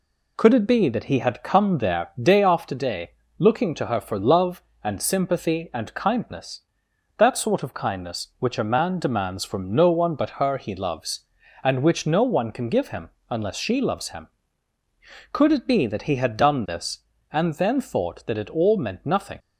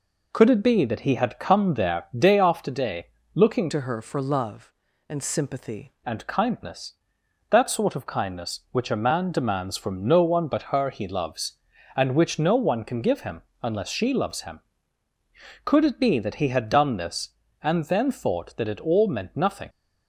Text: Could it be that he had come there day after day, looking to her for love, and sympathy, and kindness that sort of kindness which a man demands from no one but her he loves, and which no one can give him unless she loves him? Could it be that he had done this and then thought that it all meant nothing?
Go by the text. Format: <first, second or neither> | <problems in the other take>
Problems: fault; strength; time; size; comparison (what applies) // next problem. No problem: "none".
first | changes voice from "to" to "sympathy"; from 3.7 to 5.9 s; 2.2 s long // pauses between "him" and "unless"; slight; at 13.4 s; 0.22 s long; slight in the first